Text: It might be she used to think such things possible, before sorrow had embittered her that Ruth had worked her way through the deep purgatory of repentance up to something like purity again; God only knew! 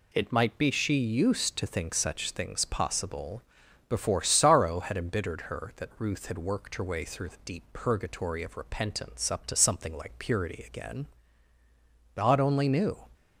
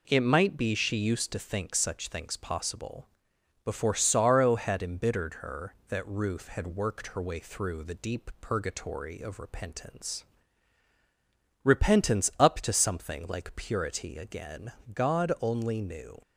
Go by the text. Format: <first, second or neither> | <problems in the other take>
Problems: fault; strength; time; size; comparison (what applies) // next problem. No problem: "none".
first | says "repentance" twice; at 11.6 s